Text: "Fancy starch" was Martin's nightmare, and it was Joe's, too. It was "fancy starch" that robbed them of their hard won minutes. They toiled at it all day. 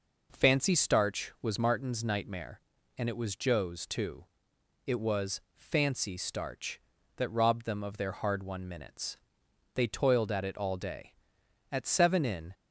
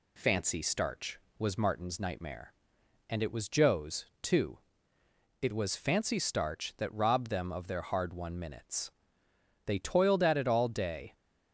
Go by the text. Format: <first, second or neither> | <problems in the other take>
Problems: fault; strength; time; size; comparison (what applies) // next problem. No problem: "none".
second | goes on to say "At seven in"; noticeable; from 11.7 s on; 0.82 s long